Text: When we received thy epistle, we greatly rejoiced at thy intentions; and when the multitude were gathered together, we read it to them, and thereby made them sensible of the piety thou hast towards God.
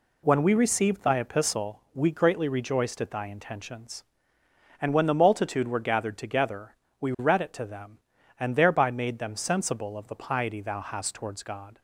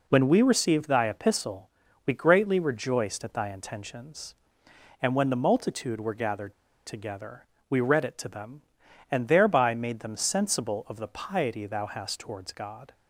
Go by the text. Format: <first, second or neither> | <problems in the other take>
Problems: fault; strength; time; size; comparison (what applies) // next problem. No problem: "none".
first | pauses between "gathered" and "together"; slight; at 6.5 s; 0.32 s long